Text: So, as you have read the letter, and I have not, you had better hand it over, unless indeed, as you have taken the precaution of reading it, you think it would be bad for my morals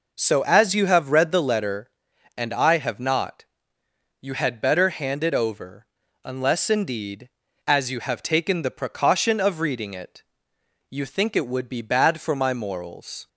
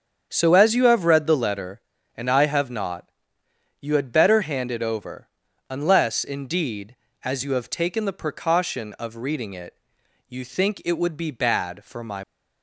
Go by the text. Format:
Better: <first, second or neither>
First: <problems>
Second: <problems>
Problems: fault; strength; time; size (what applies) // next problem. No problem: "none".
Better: first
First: none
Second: starts louder than the rest; strong; until 1.3 s; 7.5 dB // stops before "morals"; at 12.2 s